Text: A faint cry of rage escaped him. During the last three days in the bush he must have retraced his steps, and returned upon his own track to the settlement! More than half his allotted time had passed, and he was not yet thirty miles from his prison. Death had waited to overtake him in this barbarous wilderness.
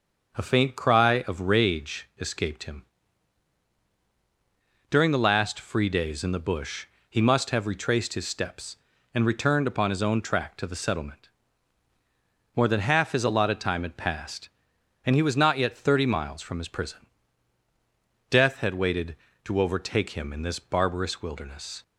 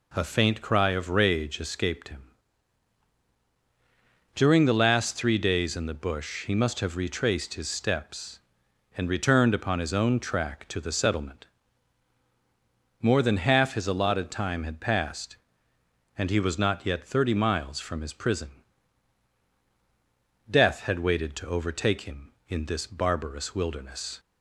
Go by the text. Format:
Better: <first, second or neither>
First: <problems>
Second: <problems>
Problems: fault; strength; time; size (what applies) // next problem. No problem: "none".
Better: second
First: starts louder than the rest; until 1.3 s; 6.5 dB // says "free" for "three"; at 5.5 s // pauses between "bush" and "he"; slight; at 6.8 s; 0.24 s long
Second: none